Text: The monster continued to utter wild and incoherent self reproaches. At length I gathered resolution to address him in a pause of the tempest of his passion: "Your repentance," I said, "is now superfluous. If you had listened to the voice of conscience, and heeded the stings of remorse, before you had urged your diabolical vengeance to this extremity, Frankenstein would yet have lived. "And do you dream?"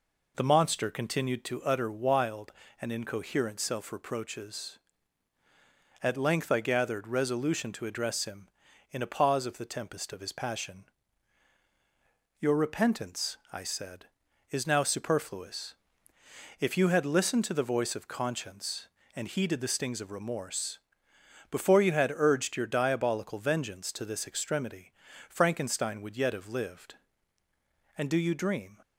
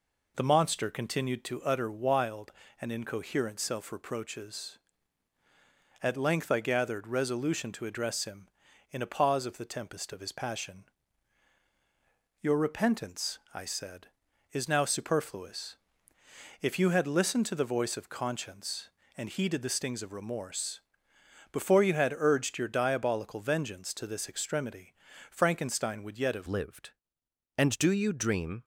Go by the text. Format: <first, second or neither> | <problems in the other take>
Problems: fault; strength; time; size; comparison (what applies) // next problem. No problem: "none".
first | changes voice at "lived"; from 26.4 s on; 2.2 s long